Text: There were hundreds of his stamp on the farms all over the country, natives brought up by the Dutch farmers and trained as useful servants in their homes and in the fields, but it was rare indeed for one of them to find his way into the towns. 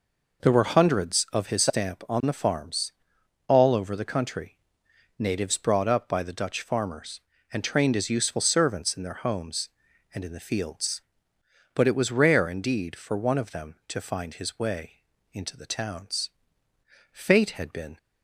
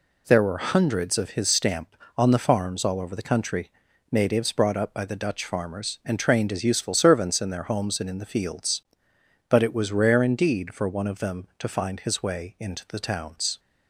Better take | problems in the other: second | pauses between "farms" and "all"; noticeable; at 2.9 s; 0.56 s long // pauses between "way" and "into"; slight; at 15.0 s; 0.28 s long // goes on to say "Fate had been"; noticeable; from 17.1 s on; 0.86 s long

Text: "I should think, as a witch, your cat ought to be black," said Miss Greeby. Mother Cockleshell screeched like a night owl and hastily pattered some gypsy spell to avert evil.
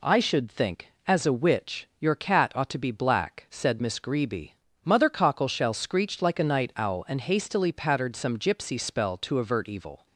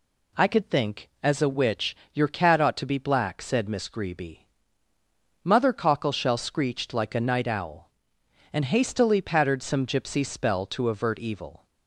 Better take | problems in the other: first | says "could" for "should"; at 0.4 s

